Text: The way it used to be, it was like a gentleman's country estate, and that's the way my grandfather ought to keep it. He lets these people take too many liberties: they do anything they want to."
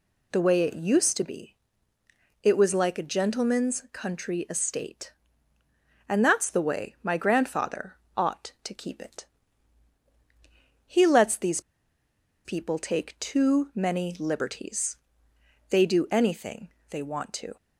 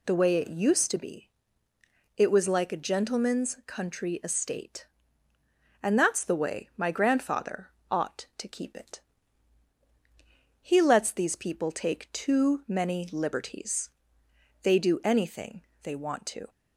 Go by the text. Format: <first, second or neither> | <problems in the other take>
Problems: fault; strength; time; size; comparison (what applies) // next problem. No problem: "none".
second | pauses between "grandfather" and "ought"; slight; at 7.9 s; 0.20 s long; slight in the second // pauses between "these" and "people"; noticeable; at 11.6 s; 0.84 s long // pauses between "anything" and "they"; slight; at 16.7 s; 0.18 s long; slight in the second